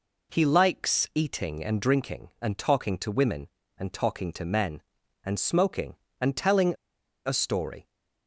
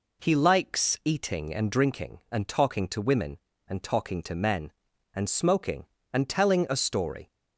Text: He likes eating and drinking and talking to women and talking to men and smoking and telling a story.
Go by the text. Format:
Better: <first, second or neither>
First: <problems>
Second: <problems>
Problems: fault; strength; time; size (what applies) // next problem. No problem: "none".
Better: second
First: pauses between "telling" and "a"; noticeable; at 6.7 s; 0.53 s long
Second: none